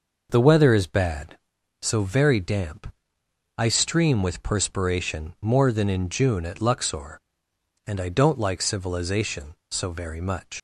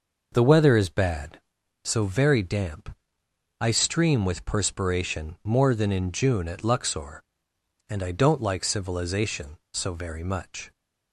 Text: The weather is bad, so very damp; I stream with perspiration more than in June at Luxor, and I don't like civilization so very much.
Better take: second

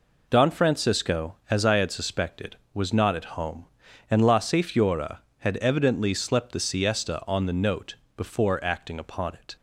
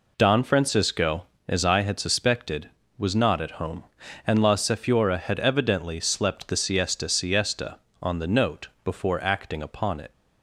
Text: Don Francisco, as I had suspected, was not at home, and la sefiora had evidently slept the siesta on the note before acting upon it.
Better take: first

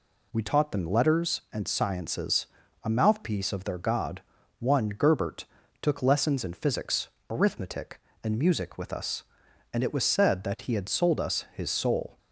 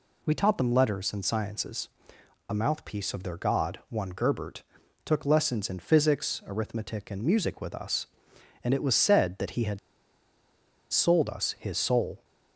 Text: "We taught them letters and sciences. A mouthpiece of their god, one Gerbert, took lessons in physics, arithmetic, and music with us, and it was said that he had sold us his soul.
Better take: first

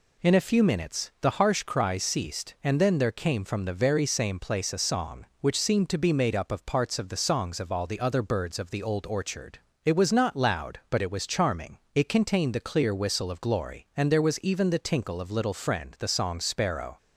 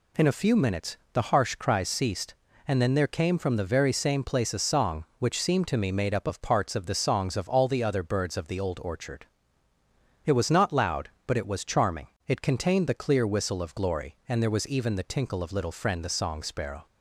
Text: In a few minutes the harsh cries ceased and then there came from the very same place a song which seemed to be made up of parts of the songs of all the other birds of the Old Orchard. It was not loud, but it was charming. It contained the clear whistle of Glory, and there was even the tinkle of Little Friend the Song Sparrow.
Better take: first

